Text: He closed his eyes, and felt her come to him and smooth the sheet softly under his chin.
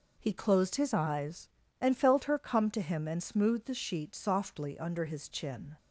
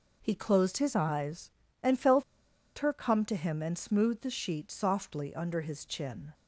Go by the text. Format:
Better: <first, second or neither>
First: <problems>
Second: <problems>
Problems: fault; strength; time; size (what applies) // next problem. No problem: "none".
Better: first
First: none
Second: pauses between "felt" and "her"; noticeable; at 2.2 s; 0.54 s long